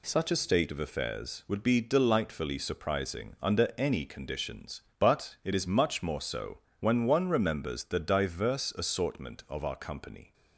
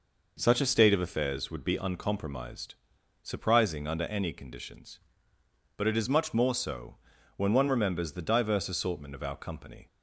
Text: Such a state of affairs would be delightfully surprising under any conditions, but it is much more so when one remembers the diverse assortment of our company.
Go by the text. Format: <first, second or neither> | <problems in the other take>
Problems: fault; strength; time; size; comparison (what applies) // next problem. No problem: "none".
first | says "uncompromised" for "delightfully"; at 1.7 s // pauses between "so" and "when"; at 6.9 s; 0.42 s long; slight in the first